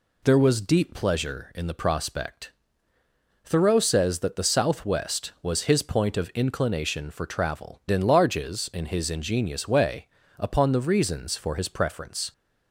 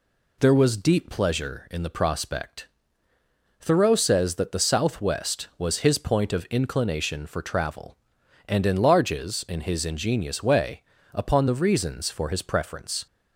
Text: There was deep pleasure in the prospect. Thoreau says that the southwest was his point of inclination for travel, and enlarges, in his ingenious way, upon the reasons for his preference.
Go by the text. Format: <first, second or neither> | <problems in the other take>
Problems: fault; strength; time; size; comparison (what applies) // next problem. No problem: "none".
second | skips "and"; at 7.8 s